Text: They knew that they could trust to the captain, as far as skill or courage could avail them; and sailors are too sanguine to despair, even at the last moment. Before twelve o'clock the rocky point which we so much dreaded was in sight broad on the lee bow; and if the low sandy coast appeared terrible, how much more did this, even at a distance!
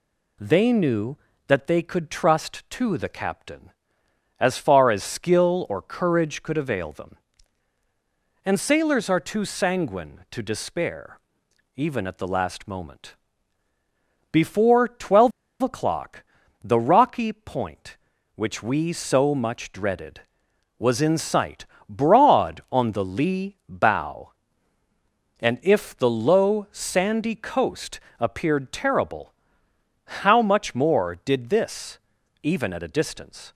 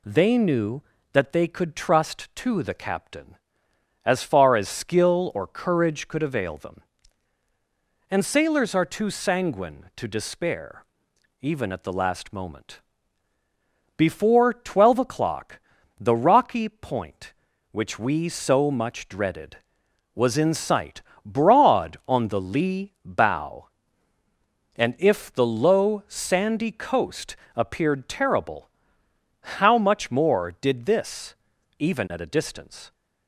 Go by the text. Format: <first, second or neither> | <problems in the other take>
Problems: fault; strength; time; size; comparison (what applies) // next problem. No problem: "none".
second | pauses between "twelve" and "o'clock"; slight; at 15.3 s; 0.30 s long // pauses between "o'clock" and "the"; at 16.2 s; 0.40 s long; also in the second // pauses between "sight" and "broad"; slight; at 21.6 s; 0.22 s long; slight in the second // pauses between "coast" and "appeared"; slight; at 27.9 s; 0.20 s long; slight in the second